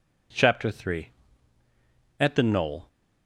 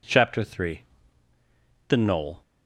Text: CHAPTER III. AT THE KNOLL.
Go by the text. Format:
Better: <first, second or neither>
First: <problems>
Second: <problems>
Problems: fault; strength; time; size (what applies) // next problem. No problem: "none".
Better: first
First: none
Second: skips "AT"; at 1.3 s